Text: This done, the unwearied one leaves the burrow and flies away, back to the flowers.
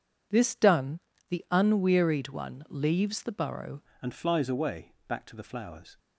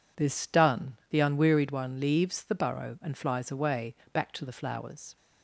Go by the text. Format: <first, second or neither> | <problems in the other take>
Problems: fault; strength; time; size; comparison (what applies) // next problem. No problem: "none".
second | changes voice at "and"; from 3.9 s on; 2.0 s long